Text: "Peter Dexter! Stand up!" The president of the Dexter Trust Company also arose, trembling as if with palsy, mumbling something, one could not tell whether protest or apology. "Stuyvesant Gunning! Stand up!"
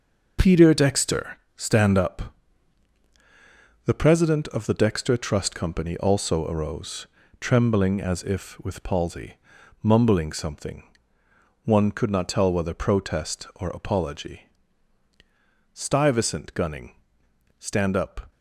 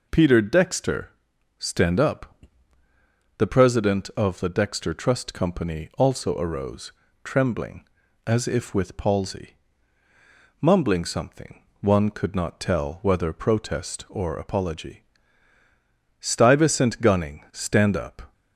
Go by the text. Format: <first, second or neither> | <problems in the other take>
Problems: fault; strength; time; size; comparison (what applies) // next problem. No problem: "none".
second | gets quieter; strong; throughout; 8 dB